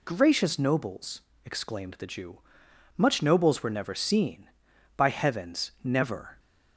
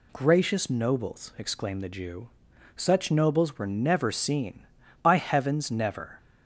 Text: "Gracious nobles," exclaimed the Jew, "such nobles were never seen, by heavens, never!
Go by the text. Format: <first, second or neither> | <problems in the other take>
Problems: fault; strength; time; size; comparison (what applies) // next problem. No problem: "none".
second | says "much" for "such"; at 2.9 s